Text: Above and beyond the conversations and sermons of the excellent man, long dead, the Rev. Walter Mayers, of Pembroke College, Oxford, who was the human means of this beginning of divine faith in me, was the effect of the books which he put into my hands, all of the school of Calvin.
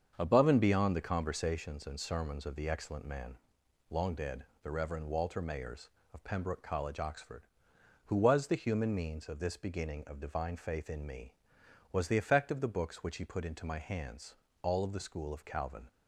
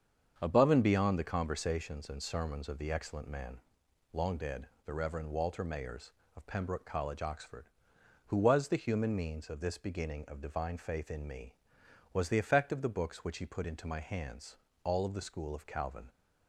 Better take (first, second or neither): neither